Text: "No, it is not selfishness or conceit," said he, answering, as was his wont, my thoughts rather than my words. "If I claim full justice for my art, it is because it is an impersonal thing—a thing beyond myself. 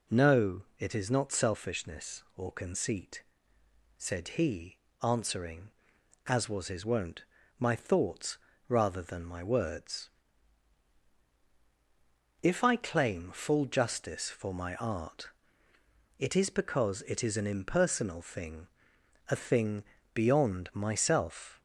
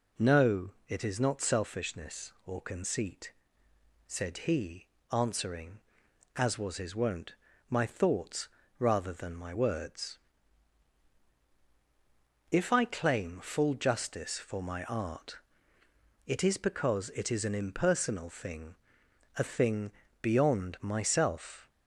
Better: neither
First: pauses between "thoughts" and "rather"; slight; at 8.3 s; 0.28 s long // pauses between "thing" and "beyond"; slight; at 19.8 s; 0.32 s long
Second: pauses between "thoughts" and "rather"; slight; at 8.4 s; 0.28 s long // pauses between "thing" and "beyond"; slight; at 19.9 s; 0.32 s long

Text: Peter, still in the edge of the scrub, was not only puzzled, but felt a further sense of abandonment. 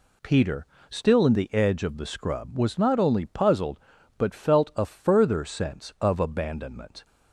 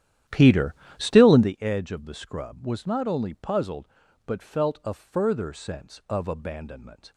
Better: first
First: none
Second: starts louder than the rest; strong; until 1.5 s; 11 dB

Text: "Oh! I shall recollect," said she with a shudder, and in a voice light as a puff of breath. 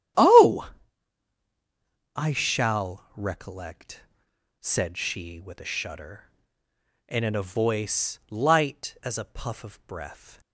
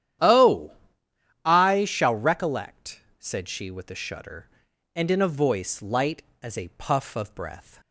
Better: neither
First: starts louder than the rest; strong; until 2.6 s; 11 dB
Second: starts louder than the rest; strong; until 1.9 s; 11 dB

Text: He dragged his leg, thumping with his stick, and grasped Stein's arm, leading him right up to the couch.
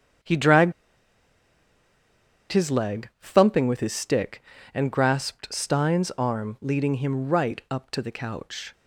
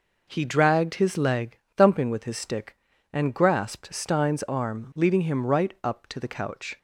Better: second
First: starts louder than the rest; strong; until 3.0 s; 7 dB // pauses between "dragged" and "his"; strong; at 0.7 s; 1.7 s long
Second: none

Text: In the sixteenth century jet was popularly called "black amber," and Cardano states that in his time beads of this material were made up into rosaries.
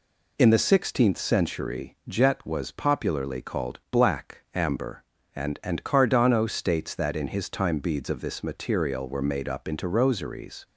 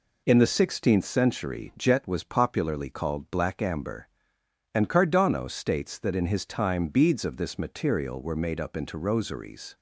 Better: second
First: says "and" twice; at 5.6 s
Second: none

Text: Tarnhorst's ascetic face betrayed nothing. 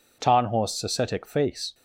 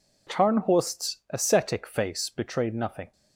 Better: second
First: stops before "betrayed nothing"; at 1.7 s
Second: none

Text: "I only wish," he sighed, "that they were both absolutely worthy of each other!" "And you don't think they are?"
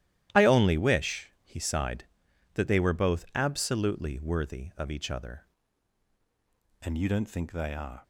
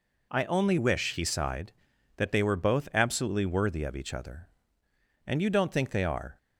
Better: second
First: starts louder than the rest; strong; until 1.4 s; 13 dB // changes voice at "And"; from 6.8 s on; 1.2 s long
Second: none

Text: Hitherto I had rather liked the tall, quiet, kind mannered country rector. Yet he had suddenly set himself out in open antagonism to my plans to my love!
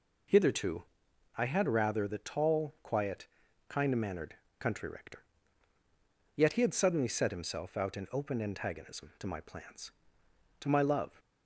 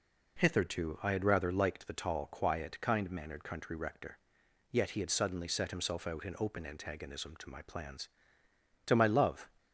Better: second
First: pauses between "Hitherto" and "I"; noticeable; at 0.8 s; 0.56 s long // skips "liked"; at 2.0 s // pauses between "mannered" and "country"; slight; at 4.3 s; 0.24 s long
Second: none

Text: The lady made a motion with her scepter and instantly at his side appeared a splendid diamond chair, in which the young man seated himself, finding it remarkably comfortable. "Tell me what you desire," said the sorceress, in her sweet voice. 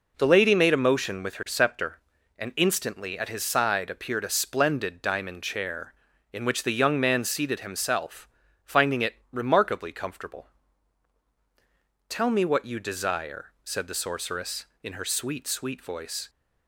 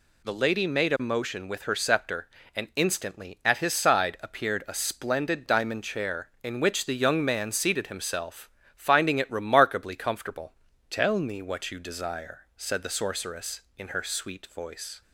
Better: second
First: pauses between "it" and "remarkably"; slight; at 9.1 s; 0.16 s long // says "sweet" twice; at 15.4 s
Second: none

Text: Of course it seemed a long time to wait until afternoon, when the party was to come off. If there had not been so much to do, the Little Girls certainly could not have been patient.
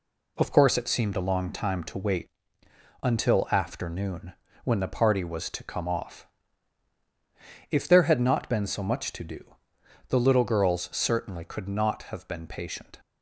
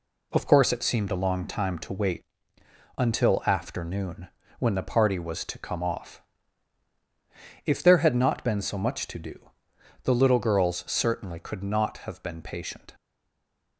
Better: first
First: pauses between "wait" and "until"; noticeable; at 2.2 s; 0.74 s long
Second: pauses between "wait" and "until"; noticeable; at 2.2 s; 0.74 s long // stays silent after the last word; slight; from 12.9 s on; 0.8 s long

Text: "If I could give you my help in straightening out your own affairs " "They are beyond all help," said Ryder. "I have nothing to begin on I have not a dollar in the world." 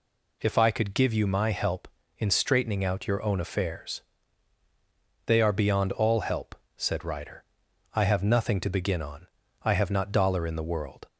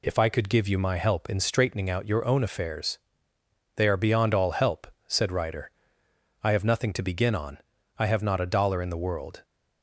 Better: second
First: pauses between "on" and "I"; slight; at 9.2 s; 0.34 s long // skips "a"; at 10.1 s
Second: pauses between "on" and "I"; at 7.5 s; 0.40 s long

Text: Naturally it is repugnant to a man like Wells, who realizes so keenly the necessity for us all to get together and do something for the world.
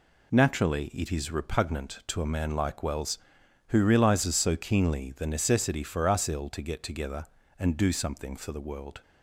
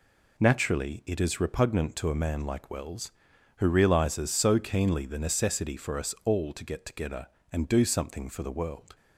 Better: second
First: says "ill" for "all"; at 6.2 s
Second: none

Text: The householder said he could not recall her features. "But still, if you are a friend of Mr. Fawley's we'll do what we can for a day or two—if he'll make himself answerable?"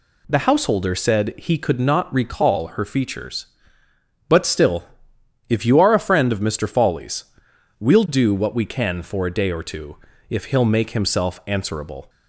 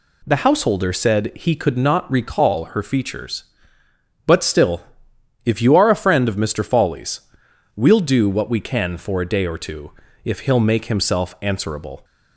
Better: neither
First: pauses between "Fawley's" and "we'll"; noticeable; at 7.2 s; 0.54 s long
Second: pauses between "Fawley's" and "we'll"; noticeable; at 7.1 s; 0.54 s long

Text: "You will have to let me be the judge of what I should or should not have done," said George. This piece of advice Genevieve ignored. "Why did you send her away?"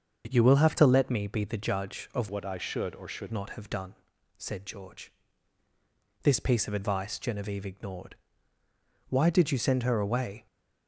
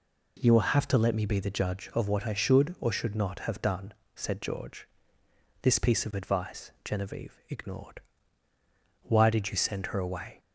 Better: second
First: starts louder than the rest; until 1.3 s; 6.5 dB // changes voice from "what" to "should"; from 2.2 to 3.3 s; 1.1 s long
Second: none

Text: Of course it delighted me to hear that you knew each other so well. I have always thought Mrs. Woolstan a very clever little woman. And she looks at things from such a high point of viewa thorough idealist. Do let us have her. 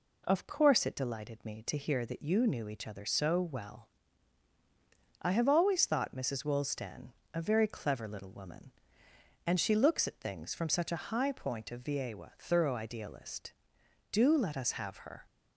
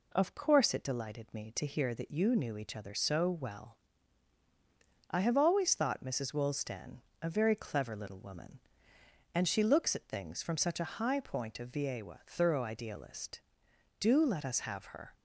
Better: neither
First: pauses between "Woolstan" and "a"; slight; at 7.0 s; 0.26 s long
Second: pauses between "Woolstan" and "a"; slight; at 6.9 s; 0.25 s long

